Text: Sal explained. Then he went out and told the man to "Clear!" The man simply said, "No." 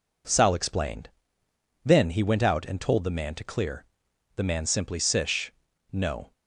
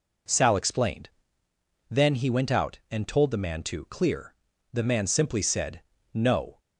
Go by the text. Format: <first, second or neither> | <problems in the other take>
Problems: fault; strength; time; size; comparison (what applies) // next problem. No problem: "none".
second | says "sish" for "said"; at 4.9 s